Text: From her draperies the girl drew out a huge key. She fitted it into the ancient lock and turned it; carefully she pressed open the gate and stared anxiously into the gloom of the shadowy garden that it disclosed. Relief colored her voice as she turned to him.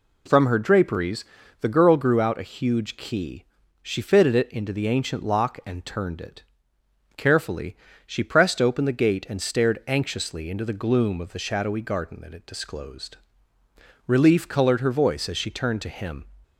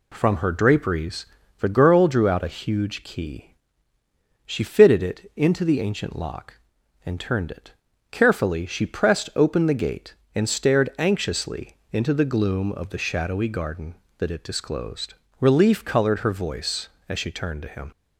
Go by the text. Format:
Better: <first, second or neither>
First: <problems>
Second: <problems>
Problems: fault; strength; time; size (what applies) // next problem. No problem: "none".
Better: second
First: pauses between "draperies" and "the"; at 1.2 s; 0.38 s long // says "grew" for "drew"; at 1.9 s // pauses between "carefully" and "she"; slight; at 7.7 s; 0.30 s long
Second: pauses between "draperies" and "the"; slight; at 1.2 s; 0.34 s long